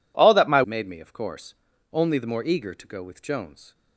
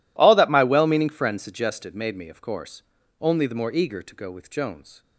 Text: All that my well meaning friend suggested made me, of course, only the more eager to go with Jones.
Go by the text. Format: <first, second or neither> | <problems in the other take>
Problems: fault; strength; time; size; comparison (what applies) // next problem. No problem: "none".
second | skips "well meaning friend suggested"; at 0.6 s